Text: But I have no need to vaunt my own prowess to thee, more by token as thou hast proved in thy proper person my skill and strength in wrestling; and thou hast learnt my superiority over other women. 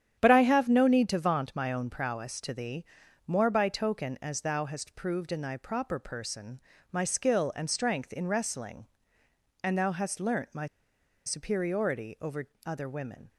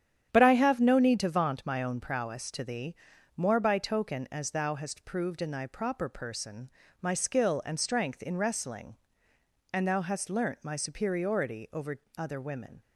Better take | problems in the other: second | starts louder than the rest; strong; until 1.2 s; 9 dB; strong in the second // pauses between "person" and "my"; slight; at 6.5 s; 0.32 s long; slight in the second // pauses between "my" and "superiority"; noticeable; at 10.6 s; 0.60 s long // pauses between "over" and "other"; slight; at 12.4 s; 0.16 s long; slight in the second

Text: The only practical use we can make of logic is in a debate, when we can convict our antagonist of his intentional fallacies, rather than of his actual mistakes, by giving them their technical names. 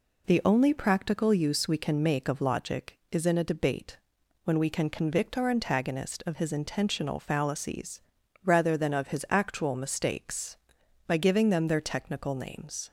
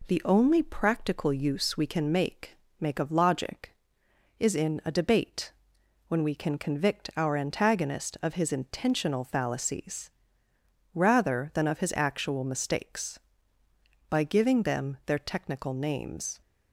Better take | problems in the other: first | says "make" twice; at 2.8 s

